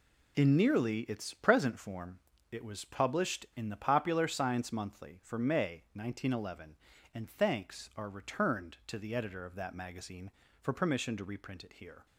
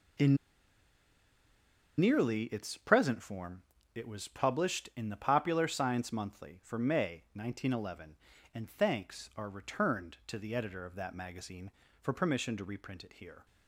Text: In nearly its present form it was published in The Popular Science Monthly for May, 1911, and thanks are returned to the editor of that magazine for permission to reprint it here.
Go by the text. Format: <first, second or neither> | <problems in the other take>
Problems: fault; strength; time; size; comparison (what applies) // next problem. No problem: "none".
first | pauses between "In" and "nearly"; strong; at 0.3 s; 1.6 s long // pauses between "form" and "it"; slight; at 3.6 s; 0.32 s long; slight in the first